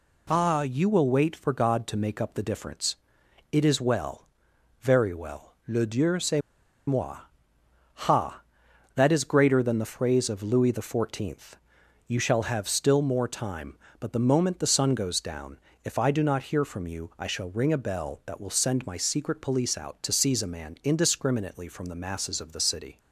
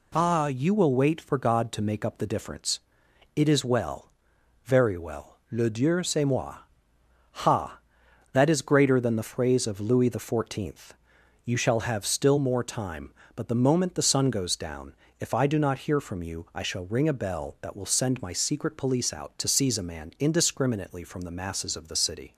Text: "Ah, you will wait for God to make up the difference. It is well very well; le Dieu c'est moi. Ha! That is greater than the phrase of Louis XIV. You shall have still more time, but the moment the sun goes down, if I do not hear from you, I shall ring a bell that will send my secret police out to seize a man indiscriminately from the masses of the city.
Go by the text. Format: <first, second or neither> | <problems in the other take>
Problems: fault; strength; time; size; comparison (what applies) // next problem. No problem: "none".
second | pauses between "well" and "very"; noticeable; at 4.2 s; 0.54 s long; noticeable in the second // pauses between "c'est" and "moi"; noticeable; at 6.4 s; 0.47 s long